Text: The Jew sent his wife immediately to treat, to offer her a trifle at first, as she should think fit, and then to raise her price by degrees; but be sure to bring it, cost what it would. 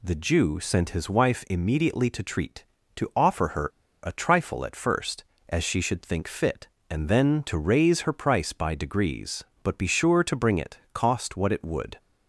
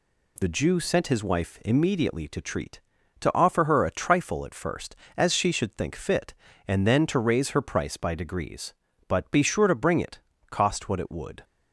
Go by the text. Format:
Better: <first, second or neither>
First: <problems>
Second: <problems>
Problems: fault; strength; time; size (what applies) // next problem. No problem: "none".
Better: second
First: pauses between "her" and "a"; at 3.6 s; 0.36 s long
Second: none